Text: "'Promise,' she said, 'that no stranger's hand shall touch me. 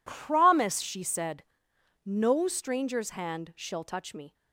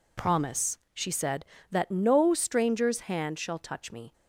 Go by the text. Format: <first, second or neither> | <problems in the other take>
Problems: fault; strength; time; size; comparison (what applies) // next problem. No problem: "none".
second | skips "that"; at 1.7 s